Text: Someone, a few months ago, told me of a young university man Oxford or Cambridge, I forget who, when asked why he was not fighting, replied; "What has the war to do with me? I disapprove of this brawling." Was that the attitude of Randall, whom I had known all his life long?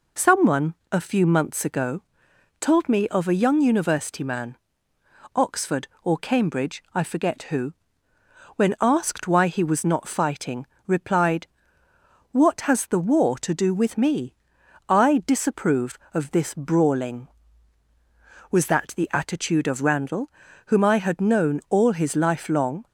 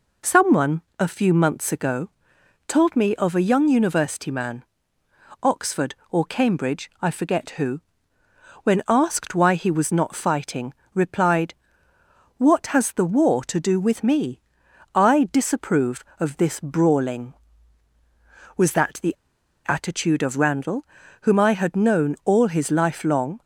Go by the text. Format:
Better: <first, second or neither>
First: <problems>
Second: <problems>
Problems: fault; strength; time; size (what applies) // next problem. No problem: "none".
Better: first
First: pauses between "man" and "Oxford"; noticeable; at 4.5 s; 0.78 s long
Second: pauses between "man" and "Oxford"; noticeable; at 4.6 s; 0.78 s long // pauses between "the" and "attitude"; noticeable; at 19.1 s; 0.51 s long